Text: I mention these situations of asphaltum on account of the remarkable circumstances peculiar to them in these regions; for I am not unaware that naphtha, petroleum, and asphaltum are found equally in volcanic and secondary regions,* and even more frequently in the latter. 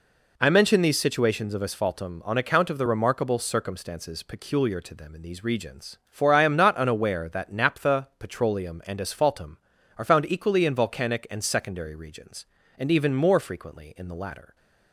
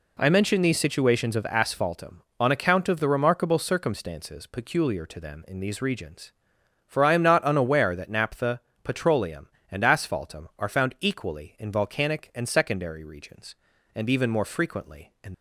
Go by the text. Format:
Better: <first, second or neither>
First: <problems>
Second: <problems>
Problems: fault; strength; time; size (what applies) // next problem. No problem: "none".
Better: first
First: none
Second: stops before "the latter"; at 15.3 s